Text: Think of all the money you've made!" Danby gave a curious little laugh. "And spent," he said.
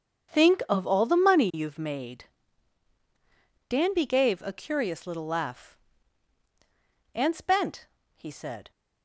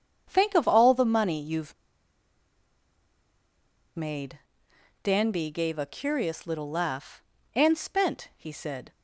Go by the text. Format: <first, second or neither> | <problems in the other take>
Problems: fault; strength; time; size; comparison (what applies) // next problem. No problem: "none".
first | starts louder than the rest; strong; until 1.3 s; 7.5 dB; strong in the first // pauses between "you've" and "made"; strong; at 1.7 s; 2.2 s long